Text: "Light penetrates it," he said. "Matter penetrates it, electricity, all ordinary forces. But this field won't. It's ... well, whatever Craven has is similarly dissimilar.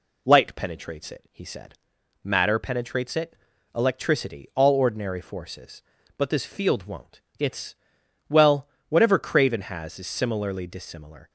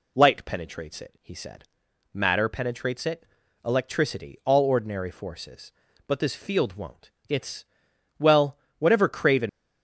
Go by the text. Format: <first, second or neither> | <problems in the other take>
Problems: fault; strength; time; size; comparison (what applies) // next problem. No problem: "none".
first | stops before "has is similarly dissimilar"; at 9.4 s